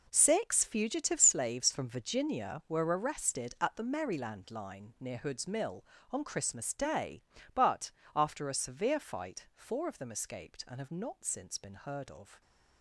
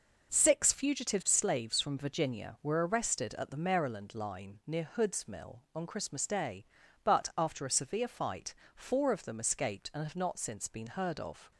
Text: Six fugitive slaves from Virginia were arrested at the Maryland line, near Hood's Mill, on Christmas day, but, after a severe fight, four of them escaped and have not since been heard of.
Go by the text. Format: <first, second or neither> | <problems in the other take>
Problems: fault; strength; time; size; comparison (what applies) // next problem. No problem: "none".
second | gets quieter; strong; throughout; 12 dB